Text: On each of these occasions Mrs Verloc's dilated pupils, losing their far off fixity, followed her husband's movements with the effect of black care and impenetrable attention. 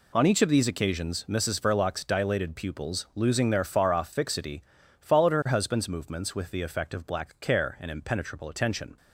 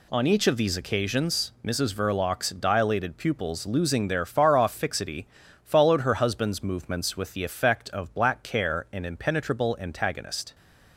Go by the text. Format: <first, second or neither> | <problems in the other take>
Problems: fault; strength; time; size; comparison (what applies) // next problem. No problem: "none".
first | says "antagonist" for "attention"; at 9.8 s